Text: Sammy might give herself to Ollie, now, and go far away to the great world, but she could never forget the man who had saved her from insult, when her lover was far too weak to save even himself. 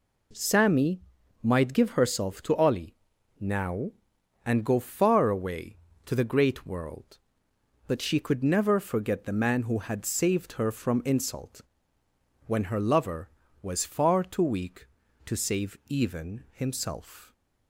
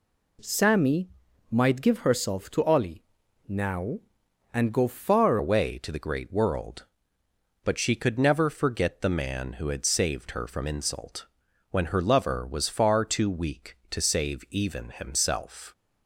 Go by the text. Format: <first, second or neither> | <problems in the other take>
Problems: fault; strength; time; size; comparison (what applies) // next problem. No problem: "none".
first | pauses between "Sammy" and "might"; at 1.0 s; 0.44 s long; also in the first // changes voice at "away"; from 5.3 s on; 10.4 s long